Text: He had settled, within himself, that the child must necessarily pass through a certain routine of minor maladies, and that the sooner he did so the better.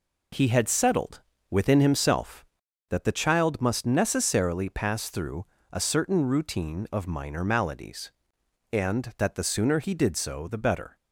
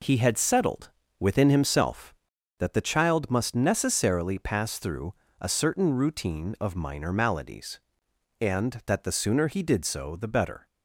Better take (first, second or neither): neither